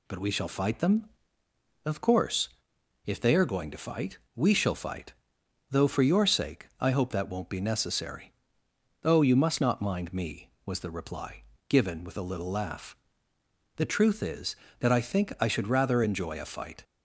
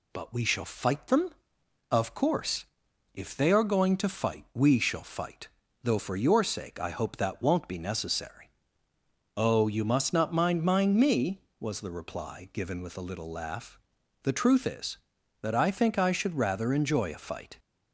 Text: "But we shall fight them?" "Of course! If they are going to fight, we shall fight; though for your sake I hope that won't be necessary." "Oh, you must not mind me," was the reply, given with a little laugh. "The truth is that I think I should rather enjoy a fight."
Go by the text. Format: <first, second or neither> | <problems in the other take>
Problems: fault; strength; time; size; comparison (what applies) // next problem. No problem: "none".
first | says "mind" twice; at 10.6 s